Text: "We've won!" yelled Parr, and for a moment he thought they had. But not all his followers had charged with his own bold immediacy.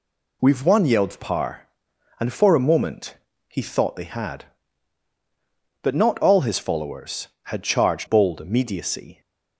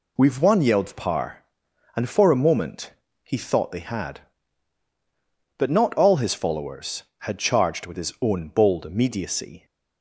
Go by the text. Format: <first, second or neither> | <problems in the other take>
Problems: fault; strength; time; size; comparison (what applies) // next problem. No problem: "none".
second | pauses between "moment" and "he"; slight; at 3.1 s; 0.34 s long; slight in the second // skips "with his own"; at 8.0 s